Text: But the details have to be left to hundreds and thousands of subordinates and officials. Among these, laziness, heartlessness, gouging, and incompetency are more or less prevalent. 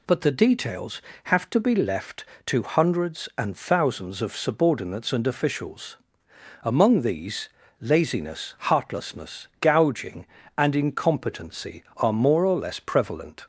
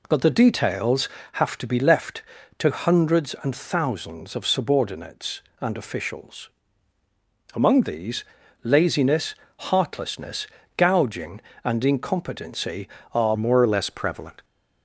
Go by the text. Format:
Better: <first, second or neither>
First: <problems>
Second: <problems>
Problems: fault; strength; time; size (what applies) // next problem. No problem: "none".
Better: first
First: none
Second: changes voice at "more"; from 13.3 s on; 1.1 s long